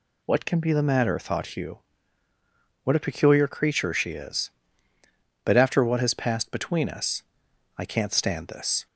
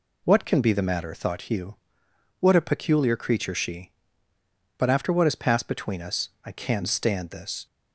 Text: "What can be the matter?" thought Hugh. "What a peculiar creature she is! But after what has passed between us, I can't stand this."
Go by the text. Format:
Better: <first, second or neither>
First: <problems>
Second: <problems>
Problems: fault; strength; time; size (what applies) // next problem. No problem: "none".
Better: first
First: none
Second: skips "is"; at 4.3 s